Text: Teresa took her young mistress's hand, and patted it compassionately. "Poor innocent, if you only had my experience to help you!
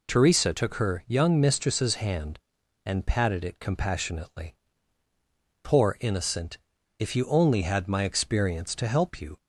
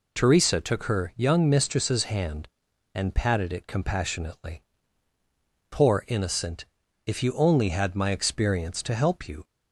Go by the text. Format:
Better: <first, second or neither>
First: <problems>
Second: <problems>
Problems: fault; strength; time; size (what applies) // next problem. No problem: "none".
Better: neither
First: none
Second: none